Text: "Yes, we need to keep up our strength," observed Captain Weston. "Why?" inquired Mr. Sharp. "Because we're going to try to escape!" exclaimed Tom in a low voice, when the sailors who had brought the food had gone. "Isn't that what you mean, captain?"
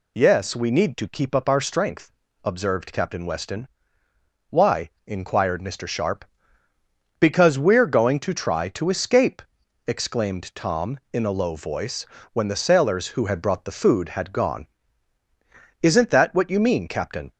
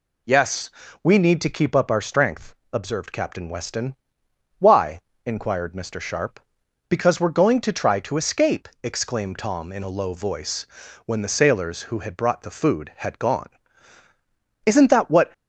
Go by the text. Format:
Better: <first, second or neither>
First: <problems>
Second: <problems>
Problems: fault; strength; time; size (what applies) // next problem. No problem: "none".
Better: first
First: none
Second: stops before "you mean captain"; at 15.3 s